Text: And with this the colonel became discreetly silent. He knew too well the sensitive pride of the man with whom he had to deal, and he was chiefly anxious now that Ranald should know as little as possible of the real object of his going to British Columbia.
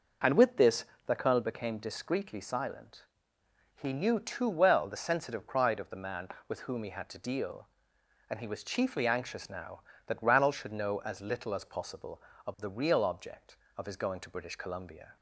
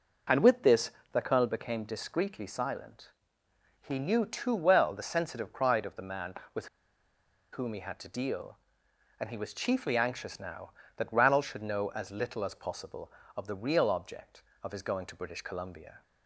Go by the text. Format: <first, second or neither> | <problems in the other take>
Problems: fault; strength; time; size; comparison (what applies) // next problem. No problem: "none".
first | pauses between "this" and "the"; slight; at 0.9 s; 0.22 s long; slight in the first // pauses between "with" and "whom"; noticeable; at 6.6 s; 0.86 s long